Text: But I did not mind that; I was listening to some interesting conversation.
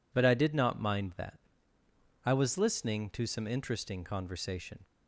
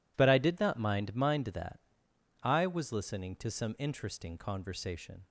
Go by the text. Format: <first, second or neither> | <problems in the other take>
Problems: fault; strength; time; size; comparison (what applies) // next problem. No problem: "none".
first | says "mind" twice; at 1.1 s